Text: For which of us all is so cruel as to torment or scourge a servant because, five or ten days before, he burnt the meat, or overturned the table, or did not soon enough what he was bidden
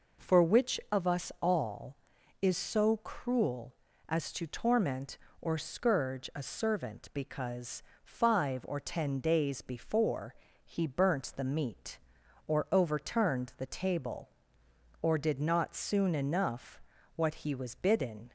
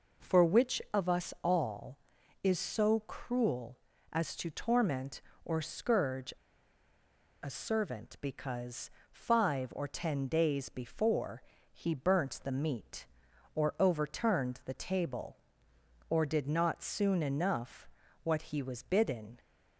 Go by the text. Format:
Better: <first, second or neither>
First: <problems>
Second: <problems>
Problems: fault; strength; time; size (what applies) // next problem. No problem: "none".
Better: first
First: pauses between "enough" and "what"; slight; at 16.8 s; 0.34 s long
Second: pauses between "scourge" and "a"; at 6.3 s; 1.1 s long // pauses between "enough" and "what"; slight; at 17.8 s; 0.34 s long